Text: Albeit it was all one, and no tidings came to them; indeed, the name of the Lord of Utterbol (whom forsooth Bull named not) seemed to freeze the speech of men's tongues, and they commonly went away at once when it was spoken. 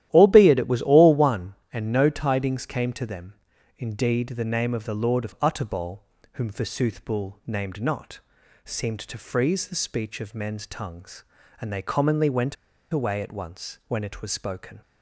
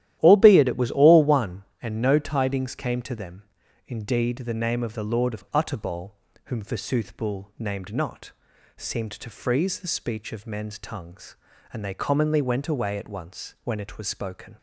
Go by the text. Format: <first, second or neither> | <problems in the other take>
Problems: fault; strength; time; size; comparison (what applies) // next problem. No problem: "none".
second | starts louder than the rest; strong; until 1.1 s; 12.5 dB; strong in the second // pauses between "went" and "away"; slight; at 12.5 s; 0.36 s long